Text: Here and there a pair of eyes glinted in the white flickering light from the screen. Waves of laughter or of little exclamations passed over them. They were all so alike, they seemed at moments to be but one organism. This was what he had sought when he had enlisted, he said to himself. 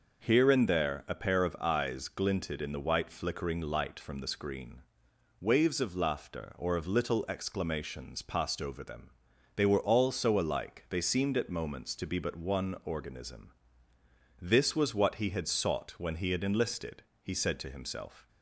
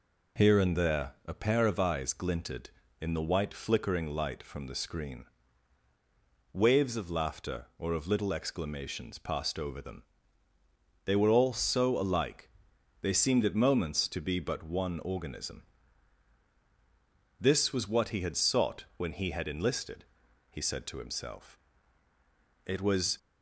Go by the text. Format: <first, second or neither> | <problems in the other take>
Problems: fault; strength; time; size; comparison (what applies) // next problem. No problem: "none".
first | goes on to say "It was"; from 22.6 s on; 0.50 s long